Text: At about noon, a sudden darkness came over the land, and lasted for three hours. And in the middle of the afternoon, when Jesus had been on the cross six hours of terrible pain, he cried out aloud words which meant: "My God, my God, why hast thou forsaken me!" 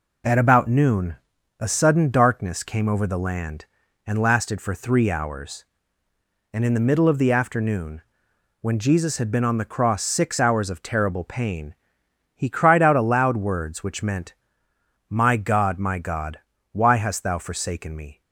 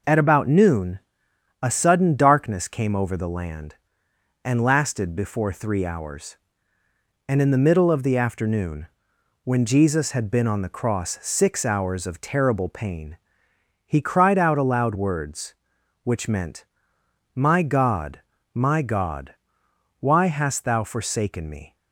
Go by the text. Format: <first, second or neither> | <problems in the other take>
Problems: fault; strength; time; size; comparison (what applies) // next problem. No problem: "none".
first | says "before" for "for"; at 5.1 s